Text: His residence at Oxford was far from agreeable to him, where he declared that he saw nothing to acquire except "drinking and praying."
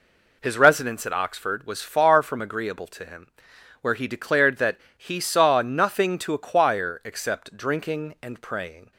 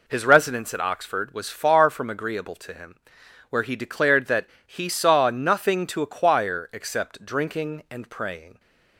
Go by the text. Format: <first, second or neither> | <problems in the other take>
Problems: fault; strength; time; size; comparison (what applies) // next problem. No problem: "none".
neither | pauses between "that" and "he"; slight; the same in both